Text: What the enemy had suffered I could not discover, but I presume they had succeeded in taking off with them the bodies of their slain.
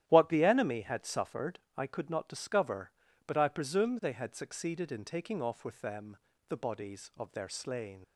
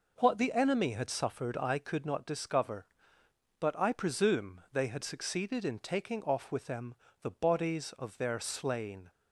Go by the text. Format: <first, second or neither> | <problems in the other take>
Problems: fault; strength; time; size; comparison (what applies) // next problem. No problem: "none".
second | starts louder than the rest; strong; until 1.0 s; 12 dB // pauses between "suffered" and "I"; slight; at 1.5 s; 0.18 s long // pauses between "them" and "the"; slight; at 6.1 s; 0.32 s long; slight in the second // leaves "slain" unfinished; at 8.0 s; 95 ms